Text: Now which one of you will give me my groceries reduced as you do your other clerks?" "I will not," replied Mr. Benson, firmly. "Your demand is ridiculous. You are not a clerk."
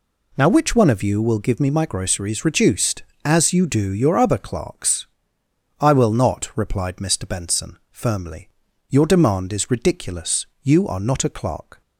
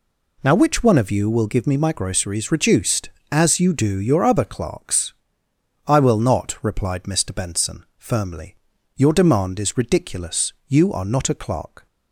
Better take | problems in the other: neither | none

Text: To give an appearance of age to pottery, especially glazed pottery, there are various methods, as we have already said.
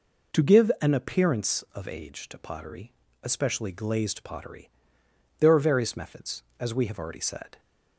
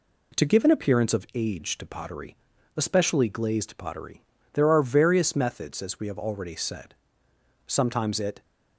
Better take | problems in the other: first | goes on to say "Sometimes it"; noticeable; from 7.6 s on; 0.76 s long

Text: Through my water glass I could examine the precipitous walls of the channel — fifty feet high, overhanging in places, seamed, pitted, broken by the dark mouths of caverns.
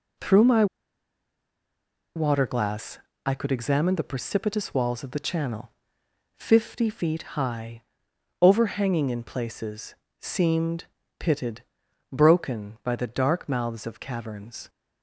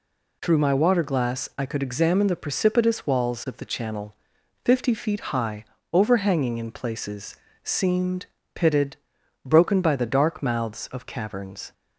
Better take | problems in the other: second | pauses between "my" and "water"; strong; at 0.6 s; 1.5 s long // pauses between "glass" and "I"; slight; at 2.9 s; 0.26 s long

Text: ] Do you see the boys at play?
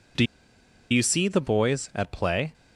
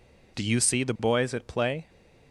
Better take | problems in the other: second | pauses between "Do" and "you"; noticeable; at 0.2 s; 0.66 s long

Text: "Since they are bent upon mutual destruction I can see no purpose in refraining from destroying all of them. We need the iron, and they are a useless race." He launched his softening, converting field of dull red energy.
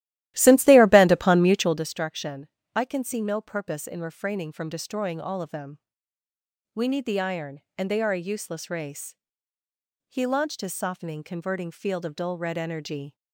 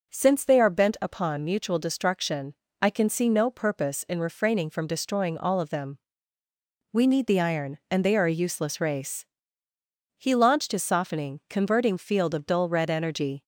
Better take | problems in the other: second | starts louder than the rest; strong; until 1.9 s; 14.5 dB // pauses between "destruction" and "I"; slight; at 2.4 s; 0.26 s long; slight in the second

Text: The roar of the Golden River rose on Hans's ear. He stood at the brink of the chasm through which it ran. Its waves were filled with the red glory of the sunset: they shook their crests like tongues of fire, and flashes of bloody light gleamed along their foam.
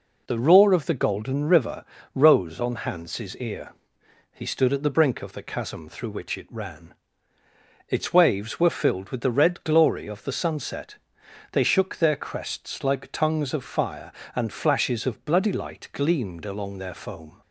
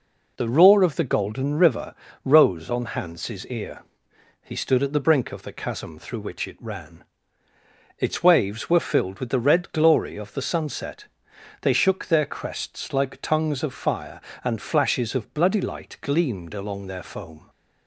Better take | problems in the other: neither | pauses between "River" and "rose"; slight; the same in both

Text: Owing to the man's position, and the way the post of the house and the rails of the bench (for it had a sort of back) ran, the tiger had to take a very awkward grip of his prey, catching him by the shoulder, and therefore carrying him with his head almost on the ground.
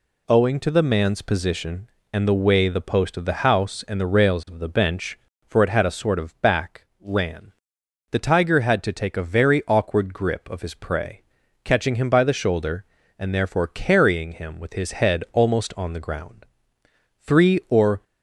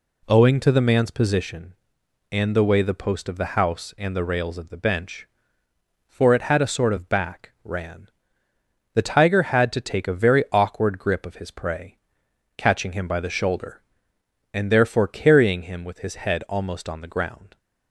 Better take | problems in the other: second | goes on to say "Three or"; noticeable; from 17.1 s on; 0.86 s long

